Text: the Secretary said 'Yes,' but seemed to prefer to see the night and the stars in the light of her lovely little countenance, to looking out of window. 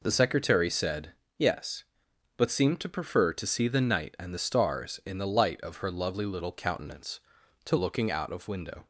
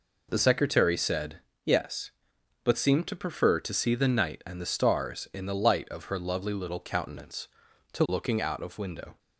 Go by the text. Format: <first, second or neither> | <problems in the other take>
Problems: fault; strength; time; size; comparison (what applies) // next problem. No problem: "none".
neither | pauses between "said" and "Yes"; slight; the same in both